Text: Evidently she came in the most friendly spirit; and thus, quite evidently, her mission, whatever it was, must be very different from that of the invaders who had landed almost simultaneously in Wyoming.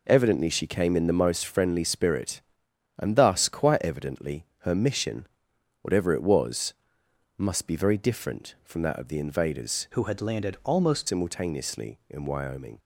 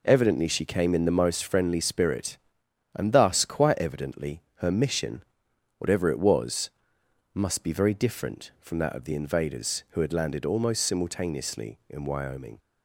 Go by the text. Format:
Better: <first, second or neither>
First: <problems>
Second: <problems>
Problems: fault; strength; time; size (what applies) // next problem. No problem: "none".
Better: second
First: changes voice from "who" to "almost"; from 9.9 to 11.0 s; 1.1 s long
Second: none